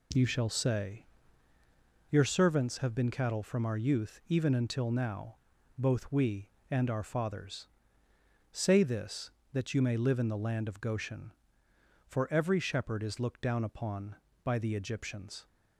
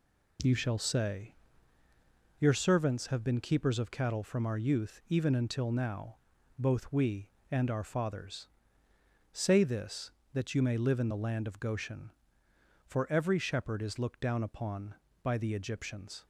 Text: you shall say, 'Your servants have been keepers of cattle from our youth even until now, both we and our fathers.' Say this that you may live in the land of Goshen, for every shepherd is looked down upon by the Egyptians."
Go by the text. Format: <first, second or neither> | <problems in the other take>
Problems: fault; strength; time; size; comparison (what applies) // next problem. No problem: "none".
second | skips "keepers of"; at 3.1 s